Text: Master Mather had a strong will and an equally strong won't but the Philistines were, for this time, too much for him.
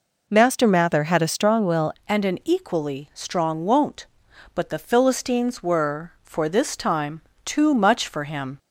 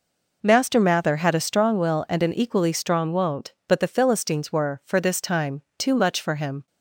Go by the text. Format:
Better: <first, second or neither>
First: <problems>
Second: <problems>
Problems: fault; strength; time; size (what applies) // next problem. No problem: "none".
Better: second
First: changes voice at "and"; from 2.0 s on; 6.5 s long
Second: none